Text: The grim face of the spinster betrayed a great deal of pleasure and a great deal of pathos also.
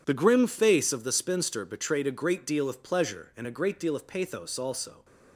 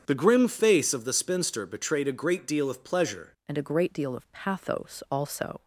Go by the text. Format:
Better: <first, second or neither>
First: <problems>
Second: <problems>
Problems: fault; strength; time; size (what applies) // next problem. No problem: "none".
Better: first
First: none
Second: starts louder than the rest; strong; until 1.0 s; 8 dB // changes voice at "and"; from 3.4 s on; 2.2 s long